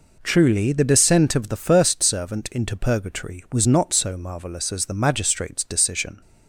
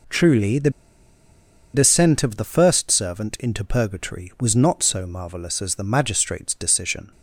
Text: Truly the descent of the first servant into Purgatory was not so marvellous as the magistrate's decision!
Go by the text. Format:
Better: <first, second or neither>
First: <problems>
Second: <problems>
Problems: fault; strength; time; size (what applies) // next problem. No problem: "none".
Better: first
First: none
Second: pauses between "the" and "descent"; at 0.6 s; 1.0 s long